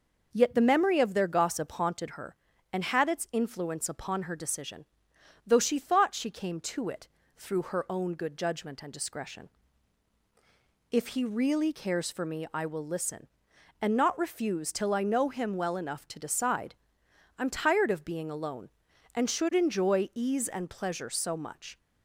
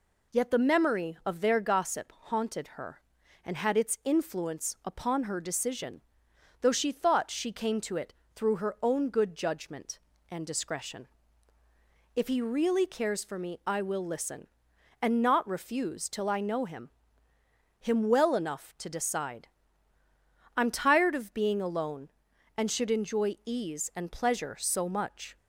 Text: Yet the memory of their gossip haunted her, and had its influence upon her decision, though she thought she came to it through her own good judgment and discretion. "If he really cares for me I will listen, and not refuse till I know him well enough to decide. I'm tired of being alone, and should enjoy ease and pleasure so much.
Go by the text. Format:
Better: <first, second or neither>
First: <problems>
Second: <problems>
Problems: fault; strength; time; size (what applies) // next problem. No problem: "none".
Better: first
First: pauses between "it" and "through"; slight; at 7.0 s; 0.28 s long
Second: pauses between "it" and "through"; slight; at 8.1 s; 0.22 s long // says "him" twice; at 17.7 s